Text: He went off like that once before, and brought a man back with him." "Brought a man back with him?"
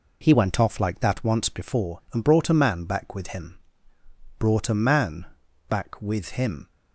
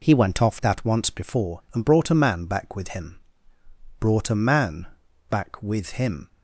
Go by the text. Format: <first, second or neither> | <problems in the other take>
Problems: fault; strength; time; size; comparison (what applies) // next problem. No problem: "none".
first | skips "like"; at 0.5 s // pauses between "man" and "back"; at 4.8 s; 0.42 s long; also in the first